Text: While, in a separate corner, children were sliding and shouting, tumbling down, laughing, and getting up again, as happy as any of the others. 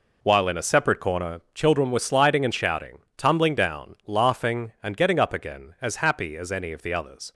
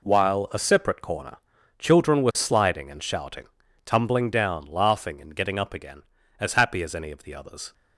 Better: first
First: none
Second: skips "in"; at 0.5 s

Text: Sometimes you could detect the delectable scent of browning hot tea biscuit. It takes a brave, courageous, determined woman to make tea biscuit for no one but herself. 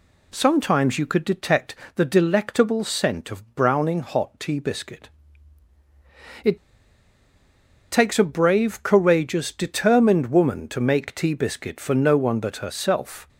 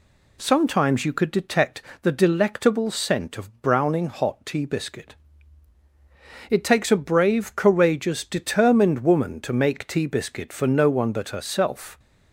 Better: second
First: pauses between "detect" and "the"; slight; at 1.7 s; 0.20 s long // pauses between "It" and "takes"; strong; at 6.5 s; 1.3 s long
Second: pauses between "detect" and "the"; slight; at 1.8 s; 0.20 s long

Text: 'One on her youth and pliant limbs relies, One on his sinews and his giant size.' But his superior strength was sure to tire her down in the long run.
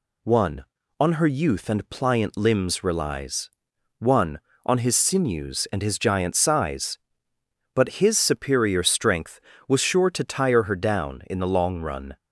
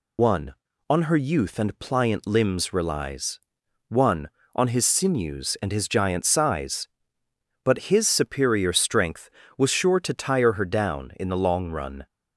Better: first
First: none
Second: loses the start of "One"; at 0.1 s; 70 ms

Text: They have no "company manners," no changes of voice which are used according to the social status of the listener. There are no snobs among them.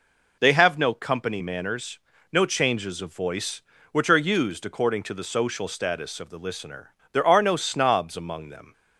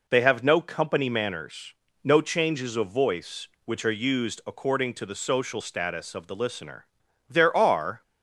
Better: first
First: none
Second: stops before "no snobs among them"; at 8.0 s

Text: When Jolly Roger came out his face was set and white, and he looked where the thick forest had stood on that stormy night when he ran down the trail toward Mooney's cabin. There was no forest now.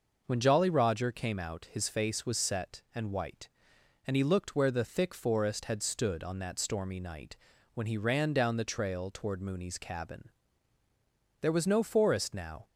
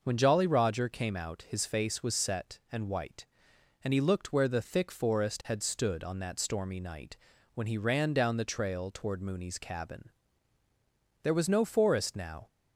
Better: neither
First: pauses between "night" and "when"; at 7.3 s; 0.38 s long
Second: pauses between "night" and "when"; at 7.1 s; 0.38 s long

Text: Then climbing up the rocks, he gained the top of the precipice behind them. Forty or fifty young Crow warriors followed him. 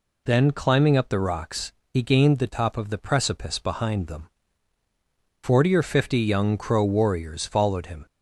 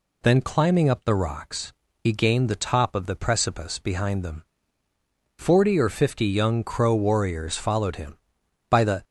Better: first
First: none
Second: goes on to say "By the"; slight; from 8.6 s on; 0.34 s long

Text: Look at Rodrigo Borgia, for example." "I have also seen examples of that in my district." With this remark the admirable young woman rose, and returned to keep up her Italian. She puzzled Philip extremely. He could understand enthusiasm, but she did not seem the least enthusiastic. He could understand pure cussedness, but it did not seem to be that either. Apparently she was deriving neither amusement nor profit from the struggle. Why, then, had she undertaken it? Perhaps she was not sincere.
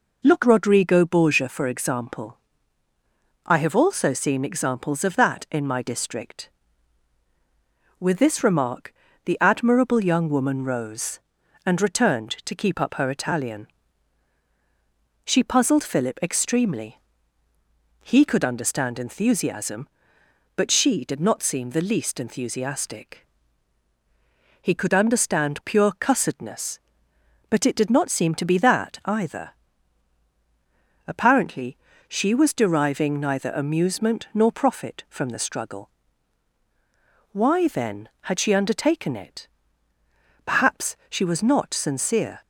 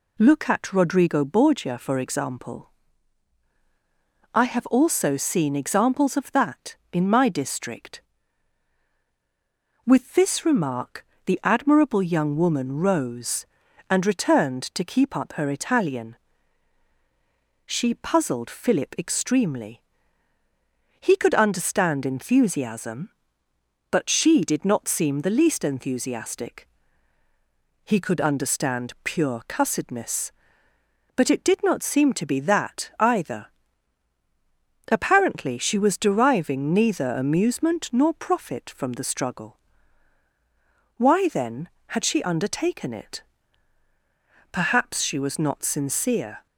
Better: second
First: skips "at"; at 0.4 s // pauses between "remark" and "the"; slight; at 8.9 s; 0.32 s long // pauses between "Apparently" and "she"; slight; at 31.7 s; 0.32 s long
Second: pauses between "remark" and "the"; slight; at 11.0 s; 0.22 s long

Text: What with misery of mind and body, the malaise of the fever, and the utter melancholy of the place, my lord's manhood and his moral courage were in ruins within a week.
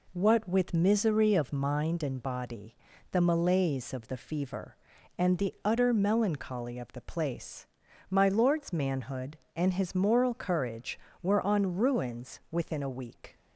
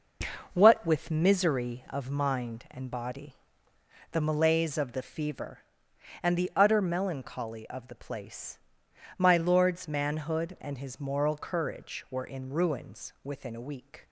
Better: second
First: says "on" for "in"; at 11.4 s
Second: none

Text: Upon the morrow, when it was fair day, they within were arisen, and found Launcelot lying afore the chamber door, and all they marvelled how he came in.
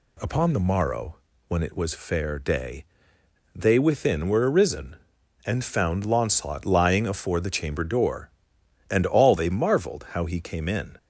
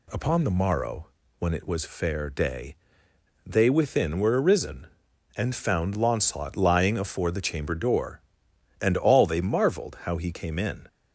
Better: neither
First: none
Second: none

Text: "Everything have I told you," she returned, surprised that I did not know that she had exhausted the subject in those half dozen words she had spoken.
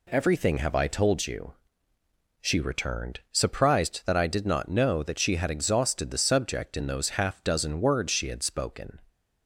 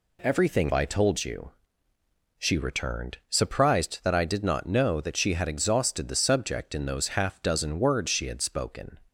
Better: first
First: none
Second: skips "have"; at 0.7 s

